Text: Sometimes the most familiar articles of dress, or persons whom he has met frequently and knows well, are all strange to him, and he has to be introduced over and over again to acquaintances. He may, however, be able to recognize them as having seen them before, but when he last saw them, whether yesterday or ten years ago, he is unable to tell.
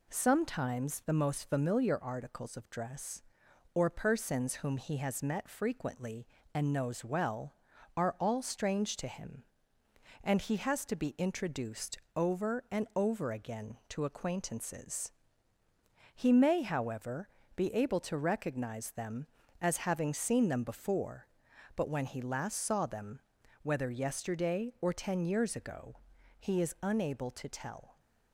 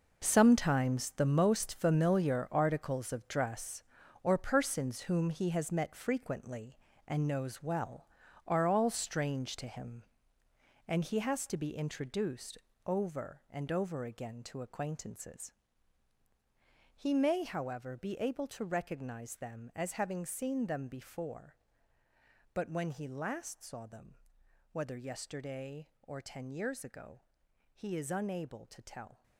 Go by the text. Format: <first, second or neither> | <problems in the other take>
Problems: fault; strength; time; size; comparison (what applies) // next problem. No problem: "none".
first | gets quieter; strong; throughout; 13 dB // pauses between "introduced" and "over"; slight; at 12.5 s; 0.30 s long; slight in the first